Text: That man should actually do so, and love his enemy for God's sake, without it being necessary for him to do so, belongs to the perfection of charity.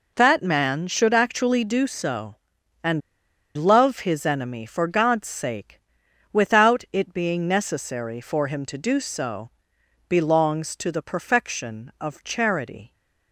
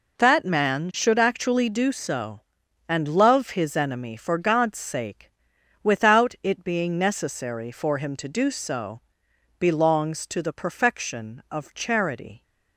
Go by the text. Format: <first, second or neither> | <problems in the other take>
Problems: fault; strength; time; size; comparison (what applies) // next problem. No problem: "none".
second | pauses between "and" and "love"; noticeable; at 3.0 s; 0.54 s long